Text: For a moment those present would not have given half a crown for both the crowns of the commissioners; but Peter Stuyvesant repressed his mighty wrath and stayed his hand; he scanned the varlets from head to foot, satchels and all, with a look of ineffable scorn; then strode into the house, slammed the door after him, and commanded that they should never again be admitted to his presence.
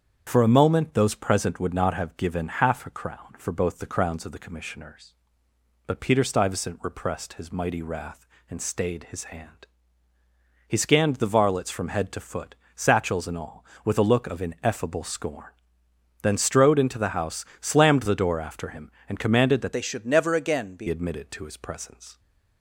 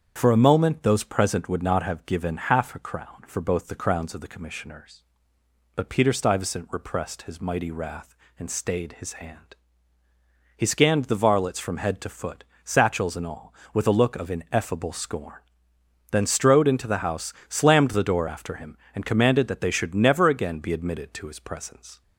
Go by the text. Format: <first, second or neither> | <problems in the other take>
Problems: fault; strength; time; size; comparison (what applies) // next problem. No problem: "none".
second | starts louder than the rest; strong; until 1.2 s; 7.5 dB; strong in the second // changes voice from "they" to "be"; from 19.7 to 20.8 s; 1.1 s long